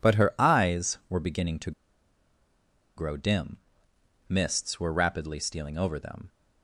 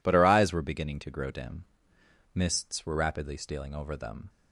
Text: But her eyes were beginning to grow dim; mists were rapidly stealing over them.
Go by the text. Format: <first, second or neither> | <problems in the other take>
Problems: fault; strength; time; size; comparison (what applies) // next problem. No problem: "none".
second | pauses between "to" and "grow"; strong; at 1.7 s; 1.2 s long